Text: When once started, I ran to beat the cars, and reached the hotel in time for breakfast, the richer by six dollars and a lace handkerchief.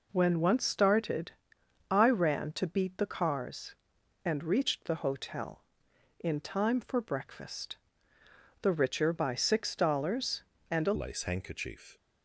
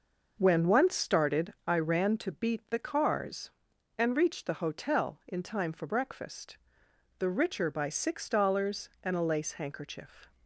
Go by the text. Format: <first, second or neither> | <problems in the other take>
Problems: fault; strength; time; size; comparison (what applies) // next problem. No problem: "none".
second | changes voice at "lace"; from 10.9 s on; 1.0 s long